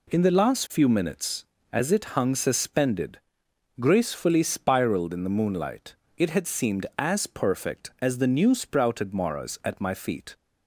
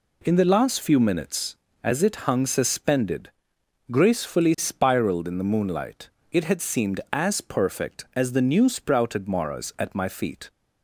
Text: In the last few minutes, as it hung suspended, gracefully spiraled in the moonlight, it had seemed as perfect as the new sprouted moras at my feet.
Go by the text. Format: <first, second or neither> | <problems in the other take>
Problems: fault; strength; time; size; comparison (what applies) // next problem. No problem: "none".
neither | none